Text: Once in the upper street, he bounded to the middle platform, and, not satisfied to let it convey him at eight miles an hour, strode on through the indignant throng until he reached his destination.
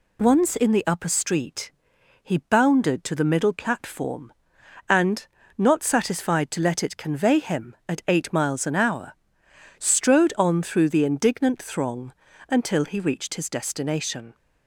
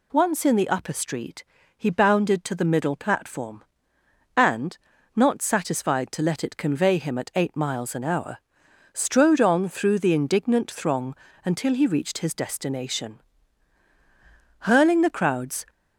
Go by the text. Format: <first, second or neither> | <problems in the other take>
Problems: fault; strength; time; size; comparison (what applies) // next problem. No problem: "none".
first | pauses between "throng" and "until"; slight; at 11.1 s; 0.32 s long; also in the first // goes on to say "Hurling the crowds"; noticeable; from 14.6 s on; 1.0 s long